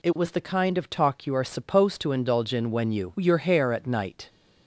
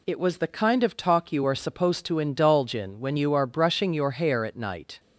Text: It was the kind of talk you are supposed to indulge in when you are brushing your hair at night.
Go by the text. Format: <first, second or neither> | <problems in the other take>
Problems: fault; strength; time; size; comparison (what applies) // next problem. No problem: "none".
second | skips "are brushing"; at 3.1 s